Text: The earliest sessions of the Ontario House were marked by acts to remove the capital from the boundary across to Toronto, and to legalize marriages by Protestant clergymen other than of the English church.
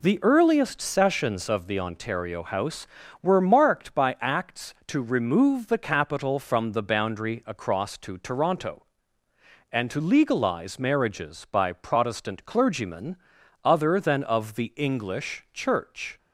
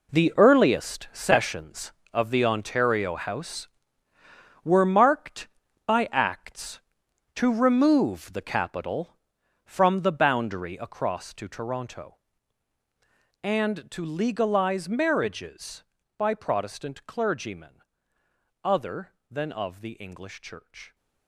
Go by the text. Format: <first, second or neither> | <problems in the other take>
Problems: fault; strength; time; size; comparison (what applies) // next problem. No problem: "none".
first | gets quieter; strong; throughout; 14 dB // pauses between "clergymen" and "other"; noticeable; at 17.8 s; 0.80 s long; noticeable in the first